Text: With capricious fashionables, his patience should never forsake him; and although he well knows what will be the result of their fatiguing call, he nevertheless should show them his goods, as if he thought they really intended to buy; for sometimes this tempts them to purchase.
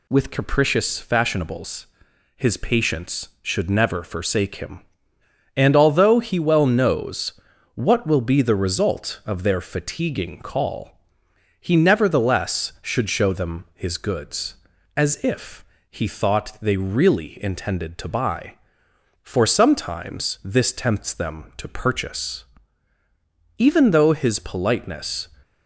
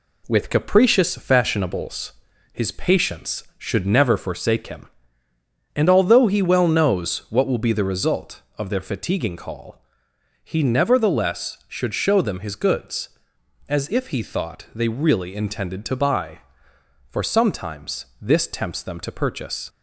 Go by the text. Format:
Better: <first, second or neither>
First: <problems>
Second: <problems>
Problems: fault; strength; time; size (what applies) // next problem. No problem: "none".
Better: second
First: pauses between "knows" and "what"; at 7.3 s; 0.42 s long // pauses between "if" and "he"; slight; at 15.6 s; 0.24 s long // goes on to say "Even though his politeness"; strong; from 23.5 s on; 1.7 s long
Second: none